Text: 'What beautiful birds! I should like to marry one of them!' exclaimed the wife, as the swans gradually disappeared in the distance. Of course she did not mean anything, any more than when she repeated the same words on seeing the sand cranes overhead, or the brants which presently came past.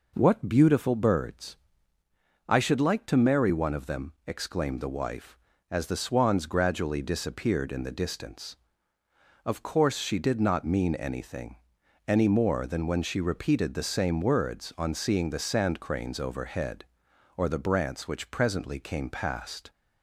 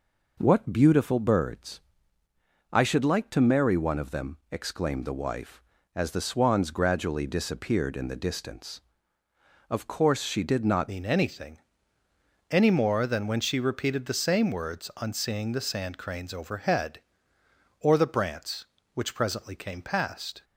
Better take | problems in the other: first | changes voice at "mean"; from 10.8 s on; 9.6 s long

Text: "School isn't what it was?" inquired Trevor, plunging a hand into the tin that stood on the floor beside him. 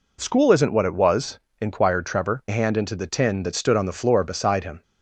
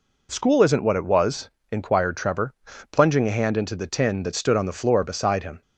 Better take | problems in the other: second | skips "plunging"; at 2.4 s

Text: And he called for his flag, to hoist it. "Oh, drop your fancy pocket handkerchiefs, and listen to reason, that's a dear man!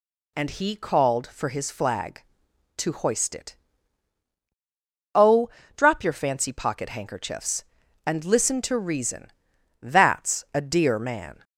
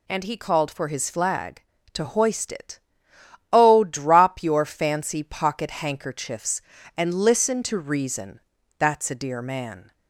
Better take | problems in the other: neither | none

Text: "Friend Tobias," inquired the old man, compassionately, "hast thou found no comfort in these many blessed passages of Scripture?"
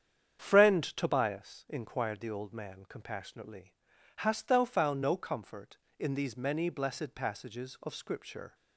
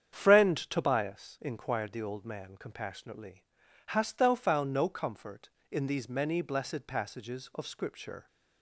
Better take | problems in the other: neither | starts louder than the rest; strong; the same in both

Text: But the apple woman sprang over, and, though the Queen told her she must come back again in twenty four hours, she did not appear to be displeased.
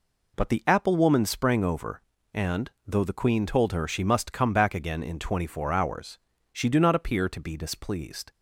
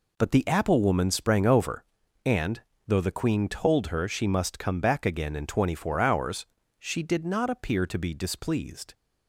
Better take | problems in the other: second | says "do" for "did"; at 6.6 s

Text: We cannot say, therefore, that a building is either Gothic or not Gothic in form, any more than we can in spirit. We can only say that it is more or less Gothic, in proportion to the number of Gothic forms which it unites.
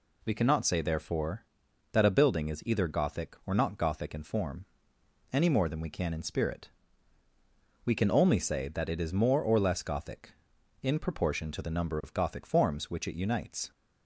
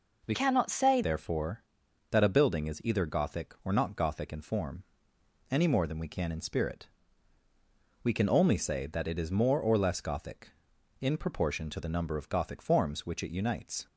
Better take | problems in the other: first | changes voice from "cannot" to "say"; from 0.3 to 1.0 s; 0.7 s long

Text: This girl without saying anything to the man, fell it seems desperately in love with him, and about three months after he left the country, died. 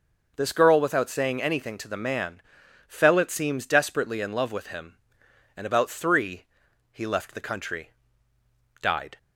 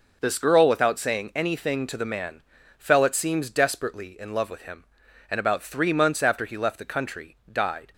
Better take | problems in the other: second | skips "months after"; at 6.6 s

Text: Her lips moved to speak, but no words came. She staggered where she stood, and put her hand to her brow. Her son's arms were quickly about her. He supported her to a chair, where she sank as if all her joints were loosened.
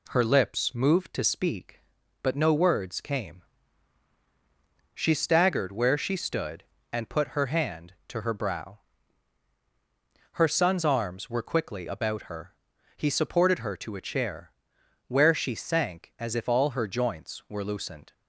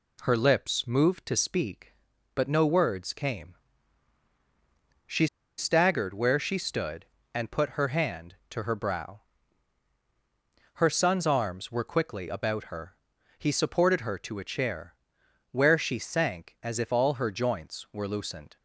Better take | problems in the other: first | pauses between "She" and "staggered"; slight; at 5.2 s; 0.30 s long

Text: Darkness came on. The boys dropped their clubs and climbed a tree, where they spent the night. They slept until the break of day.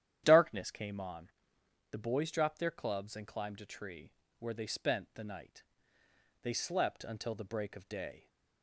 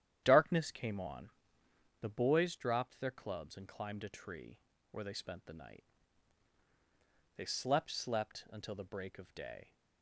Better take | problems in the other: first | starts louder than the rest; strong; until 1.2 s; 10.5 dB; strong in the first // says "slept" twice; at 7.9 s

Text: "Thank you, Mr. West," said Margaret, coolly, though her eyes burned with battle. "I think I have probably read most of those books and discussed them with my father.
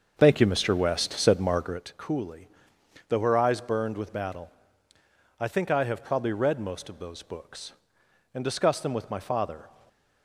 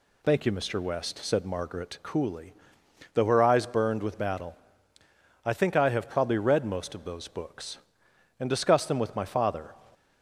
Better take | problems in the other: second | starts louder than the rest; until 1.8 s; 6.5 dB // stays silent after the last word; slight; from 9.6 s on; 0.6 s long

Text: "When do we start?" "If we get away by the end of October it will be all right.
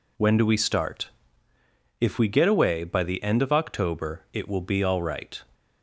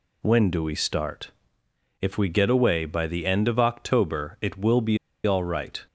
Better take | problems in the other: first | pauses between "be" and "all"; slight; at 4.9 s; 0.27 s long

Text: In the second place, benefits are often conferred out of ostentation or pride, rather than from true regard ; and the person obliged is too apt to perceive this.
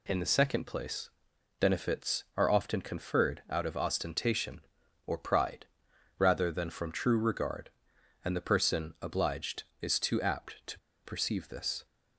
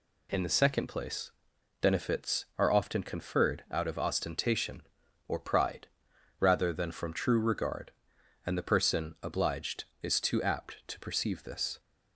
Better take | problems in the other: second | pauses between "to" and "perceive"; slight; at 10.7 s; 0.26 s long

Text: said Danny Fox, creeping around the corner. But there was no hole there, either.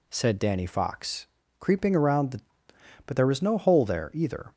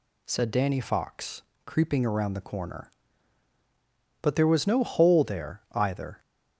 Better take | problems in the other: second | skips "corner"; at 2.7 s

